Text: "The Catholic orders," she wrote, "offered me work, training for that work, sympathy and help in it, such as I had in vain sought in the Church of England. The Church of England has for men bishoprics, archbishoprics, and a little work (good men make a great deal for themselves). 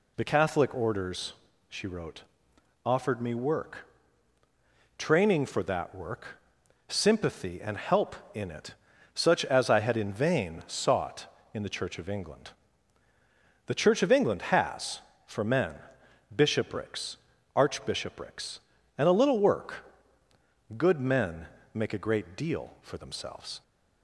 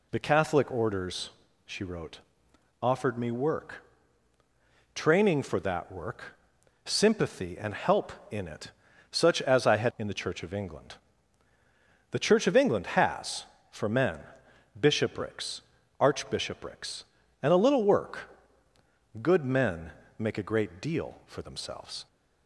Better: first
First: pauses between "men" and "bishoprics"; noticeable; at 15.7 s; 0.58 s long // pauses between "men" and "make"; slight; at 21.4 s; 0.26 s long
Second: skips "in vain sought"; at 9.9 s // pauses between "men" and "bishoprics"; noticeable; at 14.2 s; 0.58 s long // pauses between "men" and "make"; slight; at 19.9 s; 0.26 s long

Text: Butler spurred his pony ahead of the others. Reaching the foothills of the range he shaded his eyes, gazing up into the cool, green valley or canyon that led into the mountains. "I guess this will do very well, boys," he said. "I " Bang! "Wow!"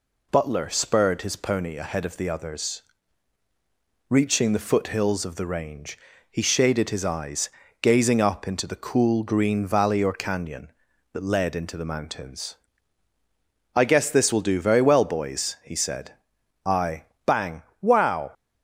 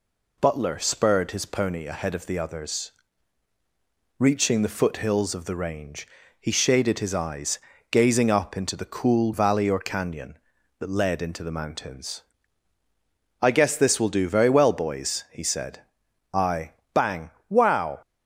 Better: first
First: pauses between "range" and "he"; slight; at 5.9 s; 0.34 s long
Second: pauses between "range" and "he"; slight; at 6.0 s; 0.34 s long // skips "green"; at 9.3 s

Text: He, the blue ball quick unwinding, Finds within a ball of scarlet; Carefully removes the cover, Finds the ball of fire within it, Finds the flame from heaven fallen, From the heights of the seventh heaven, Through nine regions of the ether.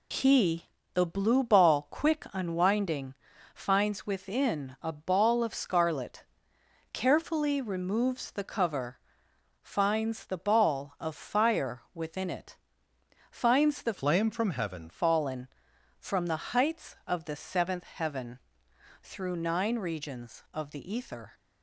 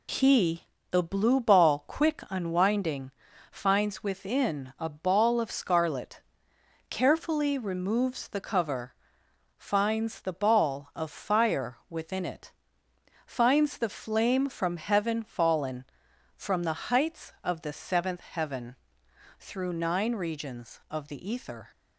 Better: second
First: changes voice from "flame" to "heaven"; from 13.9 to 14.8 s; 0.9 s long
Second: none

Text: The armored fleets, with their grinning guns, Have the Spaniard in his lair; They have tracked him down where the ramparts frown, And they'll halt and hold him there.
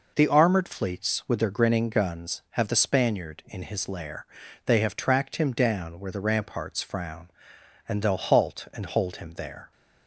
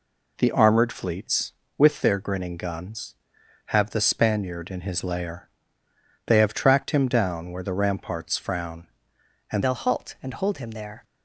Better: first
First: none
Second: changes voice at "they'll"; from 9.6 s on; 1.4 s long

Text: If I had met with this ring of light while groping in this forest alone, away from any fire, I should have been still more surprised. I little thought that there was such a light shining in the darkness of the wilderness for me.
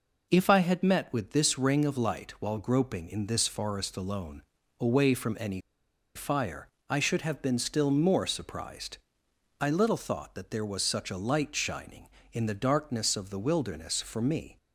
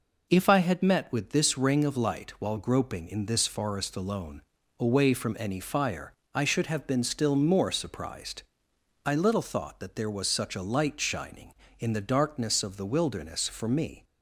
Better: second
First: pauses between "any" and "fire"; noticeable; at 5.5 s; 0.57 s long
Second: none

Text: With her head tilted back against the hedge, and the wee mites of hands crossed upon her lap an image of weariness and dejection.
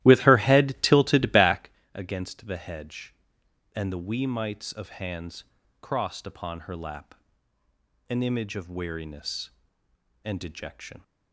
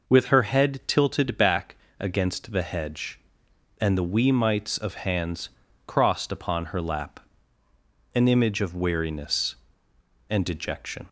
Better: second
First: starts louder than the rest; strong; until 1.8 s; 15 dB // pauses between "back" and "against"; slight; at 1.7 s; 0.22 s long // pauses between "hands" and "crossed"; at 5.4 s; 0.40 s long // pauses between "lap" and "an"; noticeable; at 7.1 s; 0.94 s long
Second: pauses between "back" and "against"; slight; at 1.7 s; 0.22 s long // pauses between "hands" and "crossed"; at 5.4 s; 0.40 s long // pauses between "lap" and "an"; noticeable; at 7.1 s; 0.94 s long

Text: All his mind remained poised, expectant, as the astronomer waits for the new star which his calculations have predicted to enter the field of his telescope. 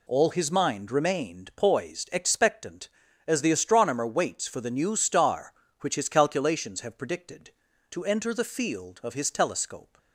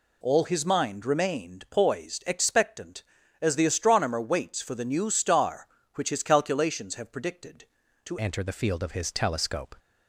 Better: first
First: none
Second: changes voice at "enter"; from 8.2 s on; 1.5 s long

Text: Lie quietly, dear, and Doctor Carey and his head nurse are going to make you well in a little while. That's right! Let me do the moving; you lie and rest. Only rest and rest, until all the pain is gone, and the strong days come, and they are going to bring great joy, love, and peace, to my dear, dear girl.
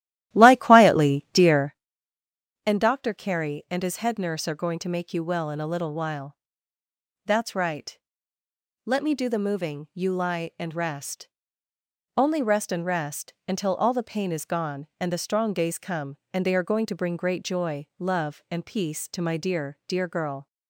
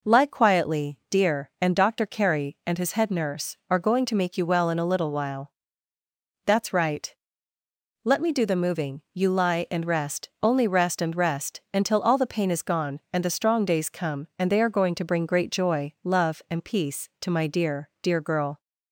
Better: second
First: starts louder than the rest; strong; until 1.9 s; 14 dB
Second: none

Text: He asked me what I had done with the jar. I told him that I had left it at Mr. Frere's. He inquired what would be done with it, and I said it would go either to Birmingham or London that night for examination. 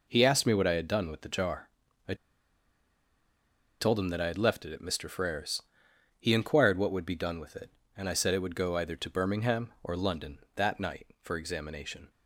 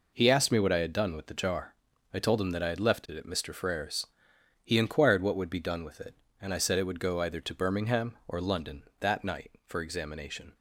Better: second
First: pauses between "I" and "told"; strong; at 2.1 s; 1.6 s long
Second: none

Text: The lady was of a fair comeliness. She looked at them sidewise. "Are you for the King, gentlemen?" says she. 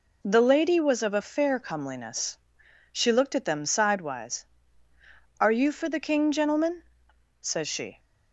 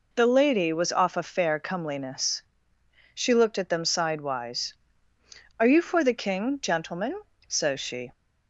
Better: first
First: none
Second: says "off" for "of"; at 0.9 s

